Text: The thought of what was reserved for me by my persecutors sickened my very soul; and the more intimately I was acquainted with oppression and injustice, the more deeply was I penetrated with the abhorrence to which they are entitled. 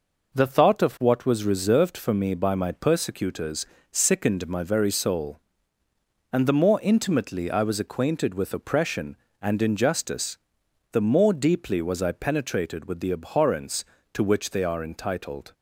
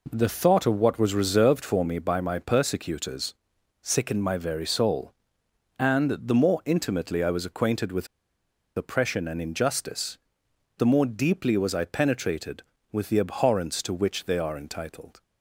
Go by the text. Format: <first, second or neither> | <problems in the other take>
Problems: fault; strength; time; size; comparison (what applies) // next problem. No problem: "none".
first | pauses between "persecutors" and "sickened"; noticeable; at 3.3 s; 0.48 s long; slight in the first // pauses between "with" and "oppression"; noticeable; at 8.0 s; 0.69 s long